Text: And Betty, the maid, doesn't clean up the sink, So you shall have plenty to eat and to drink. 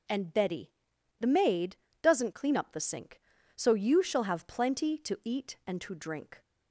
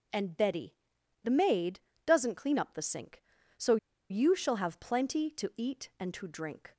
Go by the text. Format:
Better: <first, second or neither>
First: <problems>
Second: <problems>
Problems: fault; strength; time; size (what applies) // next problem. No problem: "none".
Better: first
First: none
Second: pauses between "So" and "you"; slight; at 3.7 s; 0.34 s long